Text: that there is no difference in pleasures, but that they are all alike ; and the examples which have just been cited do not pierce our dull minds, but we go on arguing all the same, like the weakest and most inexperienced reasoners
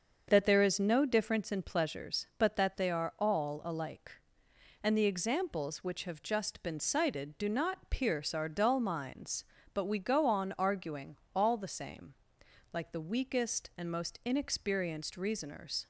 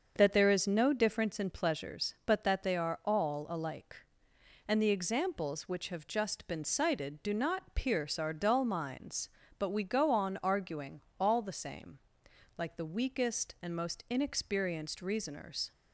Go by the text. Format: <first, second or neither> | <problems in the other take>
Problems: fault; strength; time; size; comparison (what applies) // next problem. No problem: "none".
neither | starts louder than the rest; the same in both // pauses between "arguing" and "all"; slight; the same in both